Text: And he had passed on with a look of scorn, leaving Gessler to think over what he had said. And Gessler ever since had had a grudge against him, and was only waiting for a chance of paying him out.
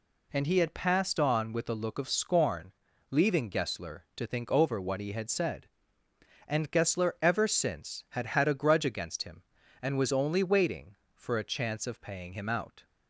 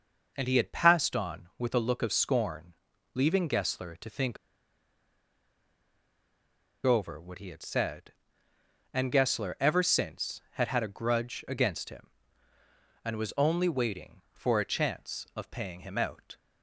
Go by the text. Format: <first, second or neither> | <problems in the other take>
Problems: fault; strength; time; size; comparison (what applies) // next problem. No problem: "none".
first | pauses between "think" and "over"; strong; at 4.3 s; 2.4 s long